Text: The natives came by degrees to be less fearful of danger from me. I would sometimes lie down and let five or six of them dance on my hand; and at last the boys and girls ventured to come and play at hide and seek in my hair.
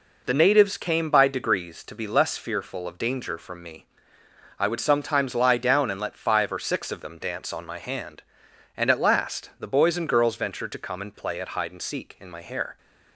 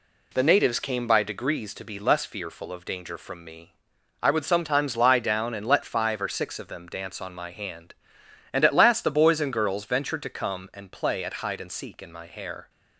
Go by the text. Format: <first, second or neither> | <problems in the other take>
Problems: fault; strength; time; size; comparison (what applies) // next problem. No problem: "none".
neither | none